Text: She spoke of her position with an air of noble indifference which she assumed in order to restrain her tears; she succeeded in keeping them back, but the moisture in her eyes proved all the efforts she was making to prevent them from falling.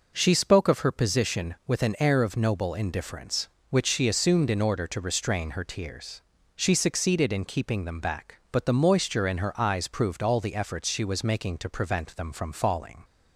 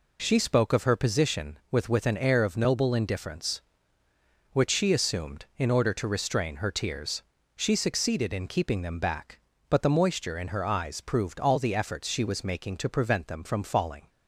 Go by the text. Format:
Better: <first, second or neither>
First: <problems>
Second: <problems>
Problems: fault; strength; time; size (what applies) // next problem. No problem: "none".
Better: first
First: none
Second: says "with" twice; at 1.8 s